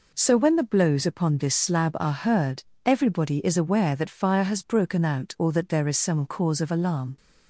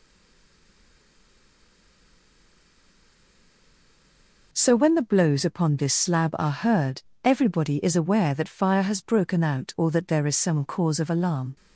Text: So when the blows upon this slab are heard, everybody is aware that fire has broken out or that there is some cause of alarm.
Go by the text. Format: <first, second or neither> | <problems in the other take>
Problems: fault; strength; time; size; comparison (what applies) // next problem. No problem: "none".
first | stays silent before the first word; strong; until 4.5 s; 4.5 s long